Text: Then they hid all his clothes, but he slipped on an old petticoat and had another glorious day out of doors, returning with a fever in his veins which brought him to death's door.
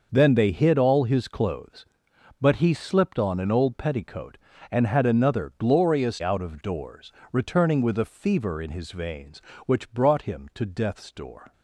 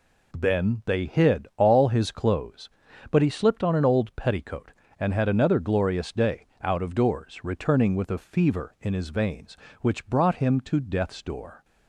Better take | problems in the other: second | skips "day"; at 6.2 s

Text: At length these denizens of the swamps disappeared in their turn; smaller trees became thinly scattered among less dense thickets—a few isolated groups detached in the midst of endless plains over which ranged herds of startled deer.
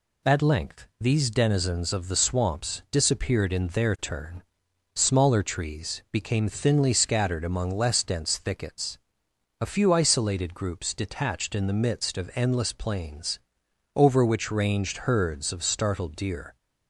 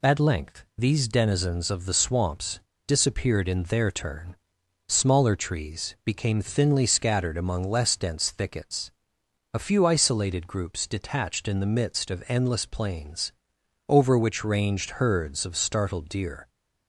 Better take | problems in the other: first | pauses between "swamps" and "disappeared"; slight; at 2.6 s; 0.26 s long // pauses between "plains" and "over"; noticeable; at 13.3 s; 0.58 s long; noticeable in the first

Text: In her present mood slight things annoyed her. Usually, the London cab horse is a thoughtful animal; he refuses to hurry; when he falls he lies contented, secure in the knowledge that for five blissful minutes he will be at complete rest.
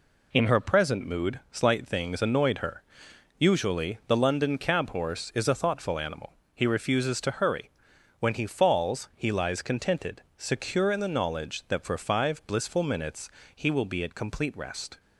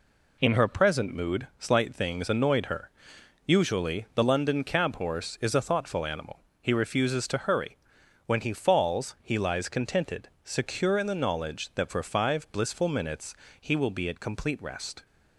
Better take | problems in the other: neither | pauses between "minutes" and "he"; slight; the same in both

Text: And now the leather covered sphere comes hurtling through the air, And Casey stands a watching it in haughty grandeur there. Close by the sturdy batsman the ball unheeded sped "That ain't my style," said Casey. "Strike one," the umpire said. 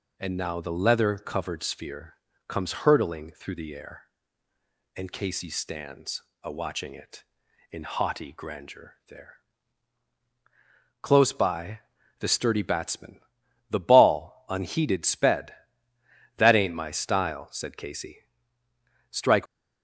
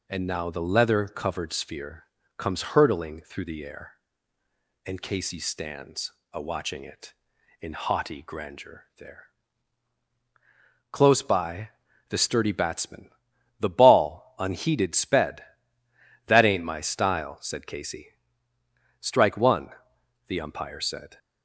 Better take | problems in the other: second | pauses between "sphere" and "comes"; slight; at 2.1 s; 0.34 s long; slight in the second // pauses between "stands" and "a"; slight; at 6.2 s; 0.20 s long; slight in the second // pauses between "by" and "the"; at 11.8 s; 0.40 s long; also in the second // pauses between "batsman" and "the"; noticeable; at 13.2 s; 0.48 s long; noticeable in the second // stops before "one the umpire said"; at 19.4 s

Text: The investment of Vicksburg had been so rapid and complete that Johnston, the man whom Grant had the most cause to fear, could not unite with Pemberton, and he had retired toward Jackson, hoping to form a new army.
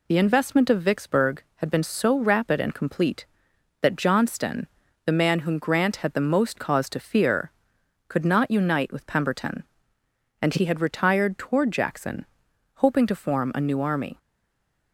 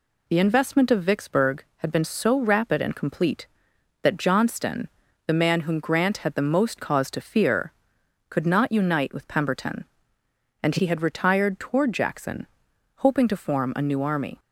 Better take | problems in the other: second | stays silent after the last word; slight; from 14.1 s on; 0.8 s long

